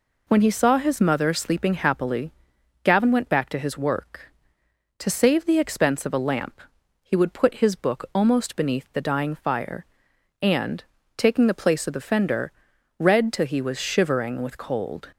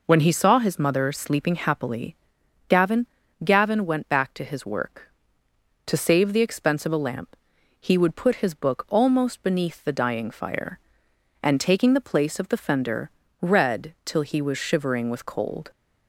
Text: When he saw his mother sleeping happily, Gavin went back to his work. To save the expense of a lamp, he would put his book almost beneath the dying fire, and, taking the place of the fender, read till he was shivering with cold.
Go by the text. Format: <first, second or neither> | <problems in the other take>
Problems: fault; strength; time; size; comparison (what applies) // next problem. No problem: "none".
first | says "Gavin" twice; at 3.4 s